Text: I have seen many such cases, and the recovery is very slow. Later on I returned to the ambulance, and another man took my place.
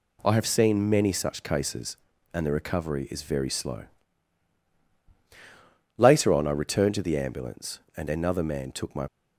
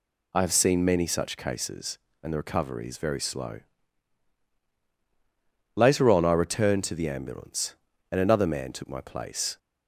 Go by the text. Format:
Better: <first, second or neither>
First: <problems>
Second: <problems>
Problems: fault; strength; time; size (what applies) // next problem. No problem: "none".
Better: second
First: stops before "place"; at 9.0 s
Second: none